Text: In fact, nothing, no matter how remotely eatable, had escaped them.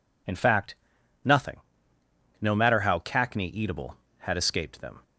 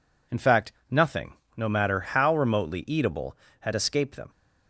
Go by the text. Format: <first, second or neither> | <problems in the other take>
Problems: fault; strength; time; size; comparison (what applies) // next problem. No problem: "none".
second | says "cackney" for "remotely"; at 2.9 s